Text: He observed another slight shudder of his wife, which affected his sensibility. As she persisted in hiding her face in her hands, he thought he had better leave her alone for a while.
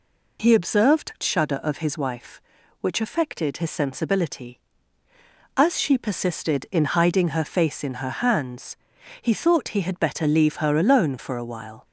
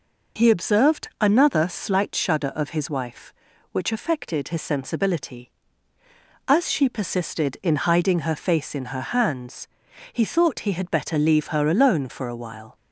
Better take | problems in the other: second | skips "another slight"; at 1.1 s

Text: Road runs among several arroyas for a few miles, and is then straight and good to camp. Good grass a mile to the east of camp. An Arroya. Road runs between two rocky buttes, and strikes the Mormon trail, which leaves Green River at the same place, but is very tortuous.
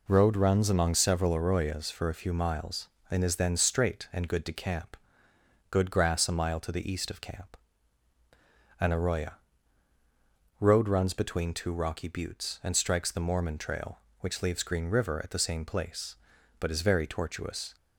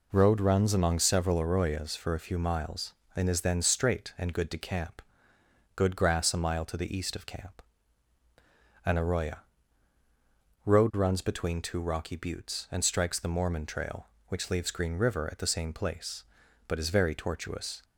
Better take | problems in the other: neither | none

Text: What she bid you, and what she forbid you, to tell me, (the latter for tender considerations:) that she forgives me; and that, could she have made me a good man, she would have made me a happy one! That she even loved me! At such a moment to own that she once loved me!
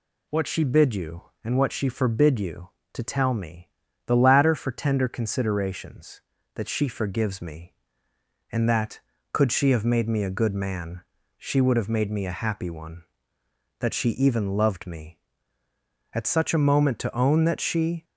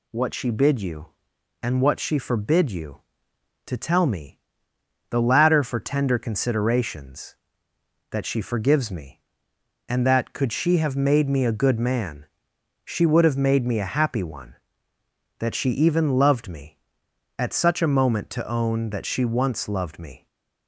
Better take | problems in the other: second | stops before "once loved me"; at 18.0 s

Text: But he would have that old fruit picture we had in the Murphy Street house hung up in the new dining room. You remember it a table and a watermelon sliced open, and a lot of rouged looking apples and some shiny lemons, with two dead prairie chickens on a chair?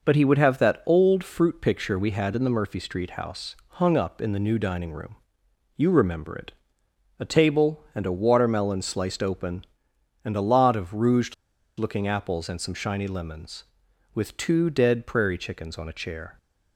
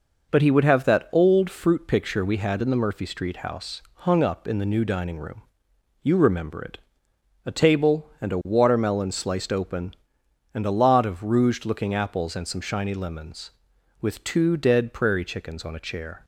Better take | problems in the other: second | pauses between "it" and "a"; noticeable; at 6.5 s; 0.66 s long; noticeable in the second // pauses between "rouged" and "looking"; at 11.3 s; 0.44 s long

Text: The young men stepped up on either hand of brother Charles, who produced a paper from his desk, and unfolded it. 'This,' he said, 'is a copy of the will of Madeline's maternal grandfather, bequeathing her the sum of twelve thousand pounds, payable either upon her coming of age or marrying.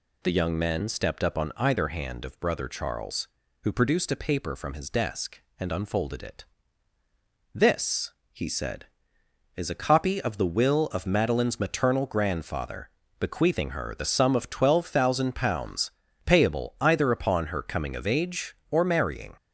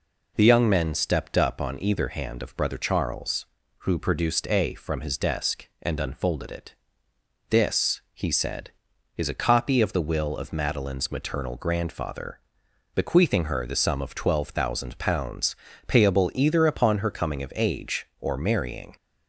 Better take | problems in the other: first | skips "paper"; at 4.7 s

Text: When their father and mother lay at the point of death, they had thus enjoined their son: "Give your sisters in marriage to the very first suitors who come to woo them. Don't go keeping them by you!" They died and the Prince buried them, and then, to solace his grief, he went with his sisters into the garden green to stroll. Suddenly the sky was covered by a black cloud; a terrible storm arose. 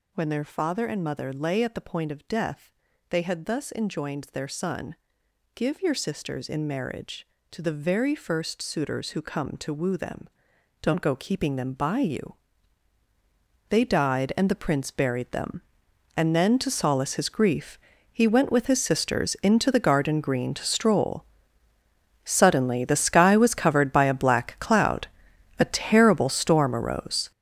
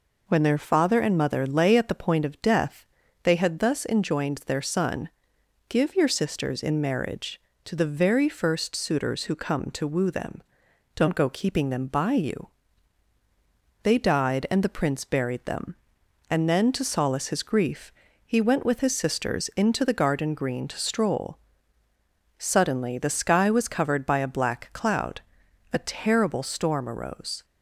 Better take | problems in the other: second | gets louder; strong; throughout; 10.5 dB

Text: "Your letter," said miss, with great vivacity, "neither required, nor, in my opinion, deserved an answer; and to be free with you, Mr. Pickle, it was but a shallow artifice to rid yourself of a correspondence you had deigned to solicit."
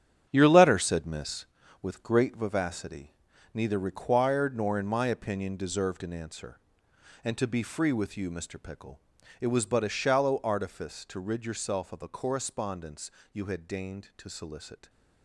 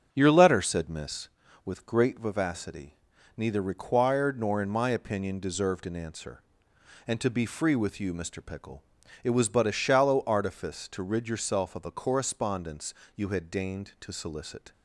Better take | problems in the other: second | gets quieter; strong; throughout; 10 dB // starts louder than the rest; strong; until 1.3 s; 9 dB; strong in the second // pauses between "correspondence" and "you"; slight; at 13.0 s; 0.22 s long; slight in the second

